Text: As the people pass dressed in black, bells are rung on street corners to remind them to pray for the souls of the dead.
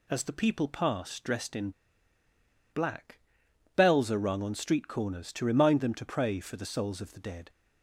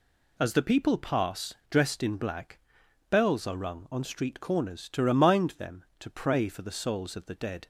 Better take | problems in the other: second | pauses between "in" and "black"; at 1.6 s; 1.0 s long

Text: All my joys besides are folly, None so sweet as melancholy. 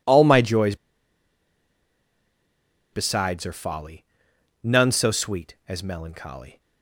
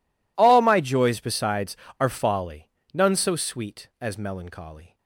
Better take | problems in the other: second | pauses between "joys" and "besides"; strong; at 0.7 s; 2.1 s long

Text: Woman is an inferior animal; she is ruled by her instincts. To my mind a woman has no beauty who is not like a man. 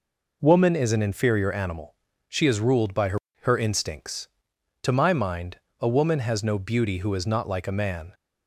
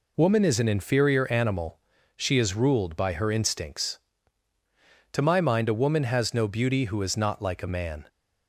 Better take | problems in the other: second | says "her" twice; at 3.4 s // pauses between "mind" and "a"; slight; at 5.5 s; 0.22 s long

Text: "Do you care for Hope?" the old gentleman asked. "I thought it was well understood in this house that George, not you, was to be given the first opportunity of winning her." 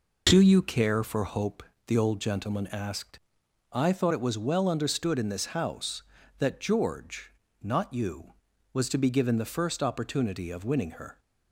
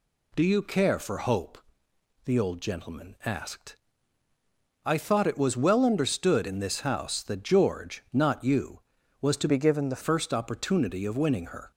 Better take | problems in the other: first | changes voice from "be" to "the"; from 9.4 to 10.0 s; 0.6 s long

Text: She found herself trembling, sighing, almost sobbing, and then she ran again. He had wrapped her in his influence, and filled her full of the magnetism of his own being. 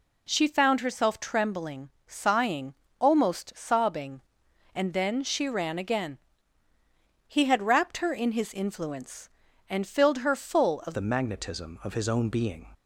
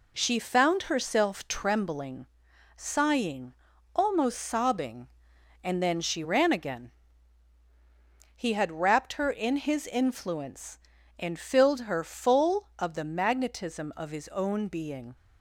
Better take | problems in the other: second | changes voice at "the"; from 10.9 s on; 1.8 s long

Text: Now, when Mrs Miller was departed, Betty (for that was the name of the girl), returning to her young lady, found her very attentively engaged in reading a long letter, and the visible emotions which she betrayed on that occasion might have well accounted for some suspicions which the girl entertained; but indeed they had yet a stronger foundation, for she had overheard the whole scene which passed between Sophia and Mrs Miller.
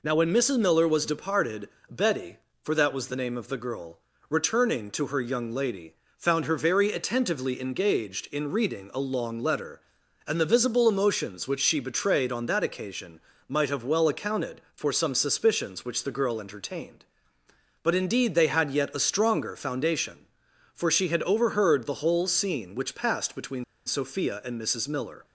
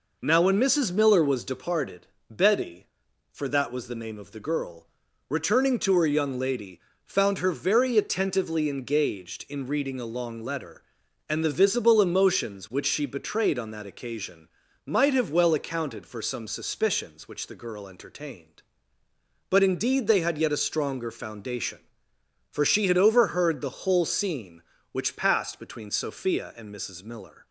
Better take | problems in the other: second | pauses between "occasion" and "might"; slight; at 13.1 s; 0.28 s long; slight in the second // pauses between "between" and "Sophia"; slight; at 23.6 s; 0.22 s long

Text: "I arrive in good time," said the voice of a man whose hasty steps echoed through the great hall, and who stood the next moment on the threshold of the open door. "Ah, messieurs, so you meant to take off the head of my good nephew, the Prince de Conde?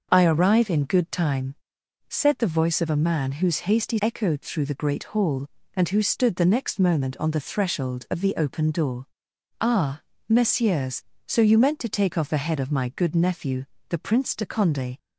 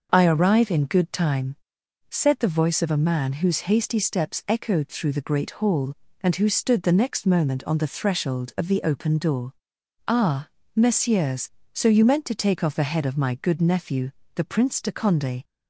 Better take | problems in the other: second | skips "steps"; at 4.0 s

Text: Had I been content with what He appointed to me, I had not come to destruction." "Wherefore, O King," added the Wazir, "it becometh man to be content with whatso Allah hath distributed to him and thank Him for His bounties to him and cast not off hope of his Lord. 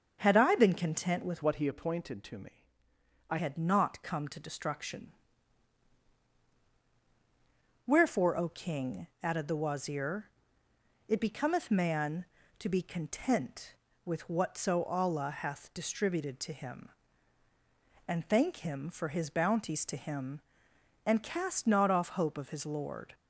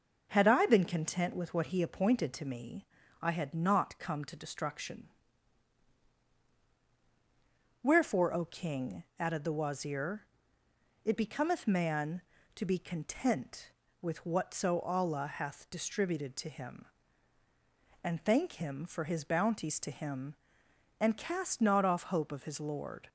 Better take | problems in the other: second | starts louder than the rest; until 1.2 s; 6.5 dB // changes voice from "what" to "I"; from 1.4 to 3.3 s; 1.9 s long

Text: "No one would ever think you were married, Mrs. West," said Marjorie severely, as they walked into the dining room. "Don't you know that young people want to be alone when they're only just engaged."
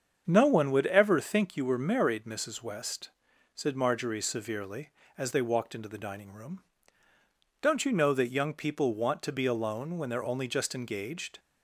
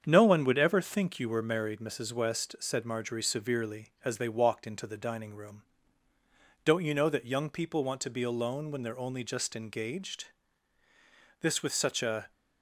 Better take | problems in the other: first | starts louder than the rest; strong; until 1.0 s; 7.5 dB; strong in the first // goes on to say "This with such a"; noticeable; from 11.3 s on; 0.92 s long

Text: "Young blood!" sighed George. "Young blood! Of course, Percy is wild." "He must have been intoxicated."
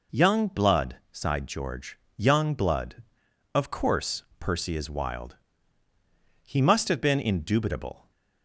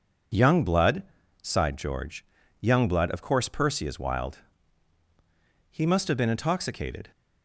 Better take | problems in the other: second | says "indubitable" for "intoxicated"; at 7.2 s

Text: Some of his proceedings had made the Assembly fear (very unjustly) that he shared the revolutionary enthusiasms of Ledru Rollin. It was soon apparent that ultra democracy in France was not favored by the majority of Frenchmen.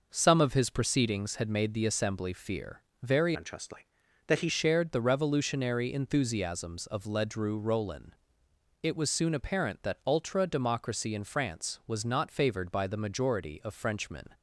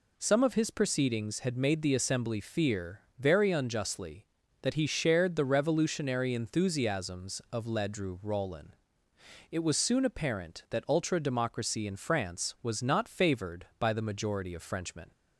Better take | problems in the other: second | changes voice from "unjustly" to "he"; from 3.3 to 4.4 s; 1.1 s long

